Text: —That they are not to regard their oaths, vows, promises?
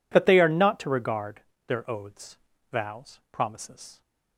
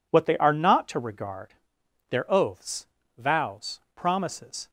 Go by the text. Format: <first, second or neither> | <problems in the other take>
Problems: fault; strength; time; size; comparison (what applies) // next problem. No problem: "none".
first | says "What" for "That"; at 0.1 s // pauses between "regard" and "their"; noticeable; at 1.5 s; 0.56 s long; slight in the first